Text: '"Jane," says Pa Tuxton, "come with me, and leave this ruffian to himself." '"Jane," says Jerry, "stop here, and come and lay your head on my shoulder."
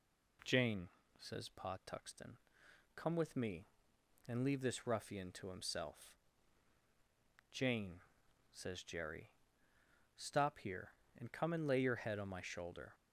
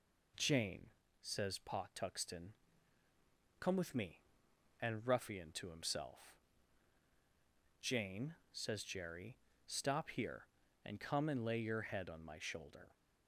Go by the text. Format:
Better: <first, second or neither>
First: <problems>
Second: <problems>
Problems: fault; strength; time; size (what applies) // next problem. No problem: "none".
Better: first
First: none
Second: skips "leave this"; at 5.0 s